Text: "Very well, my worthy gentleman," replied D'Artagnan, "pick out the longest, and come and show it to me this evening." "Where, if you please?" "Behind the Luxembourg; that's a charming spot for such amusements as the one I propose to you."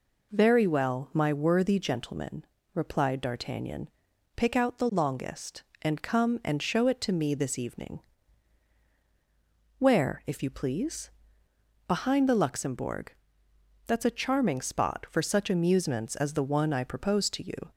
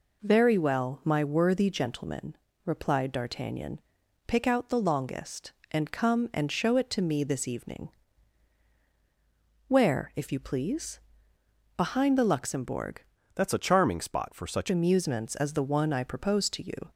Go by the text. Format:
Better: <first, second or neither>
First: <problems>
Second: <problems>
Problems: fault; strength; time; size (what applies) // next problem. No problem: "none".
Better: first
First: none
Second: changes voice from "that's" to "such"; from 13.3 to 14.6 s; 1.3 s long